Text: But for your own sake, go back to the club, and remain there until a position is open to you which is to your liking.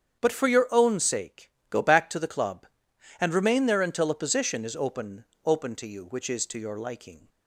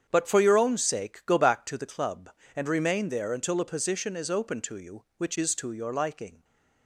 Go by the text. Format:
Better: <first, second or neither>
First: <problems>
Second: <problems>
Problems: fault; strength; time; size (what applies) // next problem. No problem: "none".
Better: second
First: starts louder than the rest; strong; until 1.2 s; 8 dB // says "open" twice; at 5.4 s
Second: starts louder than the rest; strong; until 1.0 s; 8 dB